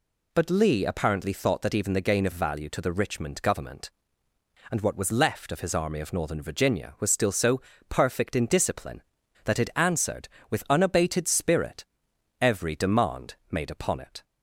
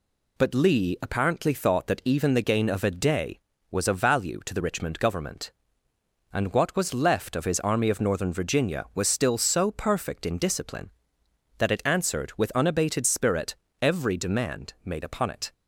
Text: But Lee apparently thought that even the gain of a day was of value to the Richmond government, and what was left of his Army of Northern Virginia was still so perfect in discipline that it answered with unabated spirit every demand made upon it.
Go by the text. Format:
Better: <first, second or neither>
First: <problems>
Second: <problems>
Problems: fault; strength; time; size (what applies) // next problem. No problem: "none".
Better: second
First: skips "a day was of"; at 2.3 s // pauses between "so" and "perfect"; slight; at 7.6 s; 0.28 s long // pauses between "spirit" and "every"; noticeable; at 11.8 s; 0.56 s long // pauses between "demand" and "made"; slight; at 13.3 s; 0.16 s long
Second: pauses between "spirit" and "every"; slight; at 13.5 s; 0.26 s long